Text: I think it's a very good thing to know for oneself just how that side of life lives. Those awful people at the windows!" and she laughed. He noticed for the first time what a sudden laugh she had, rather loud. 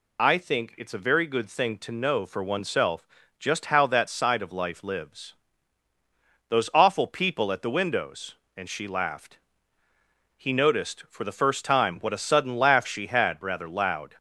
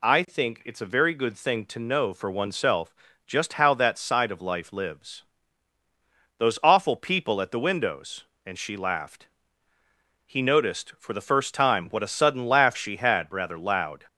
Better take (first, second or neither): second